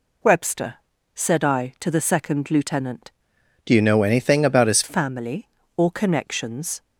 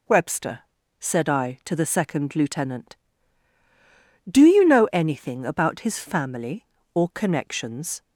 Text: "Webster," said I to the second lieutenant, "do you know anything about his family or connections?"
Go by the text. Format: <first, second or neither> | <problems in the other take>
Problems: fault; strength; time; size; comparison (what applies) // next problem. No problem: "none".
second | changes voice from "do" to "his"; from 3.6 to 4.8 s; 1.2 s long